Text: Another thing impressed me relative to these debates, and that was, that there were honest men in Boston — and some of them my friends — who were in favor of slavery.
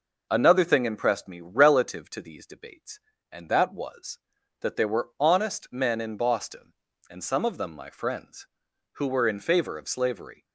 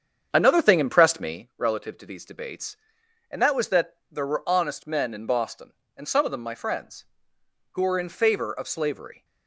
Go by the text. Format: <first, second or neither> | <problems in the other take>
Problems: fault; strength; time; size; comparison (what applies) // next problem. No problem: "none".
first | starts louder than the rest; strong; until 1.5 s; 8 dB // pauses between "that" and "there"; slight; at 3.9 s; 0.16 s long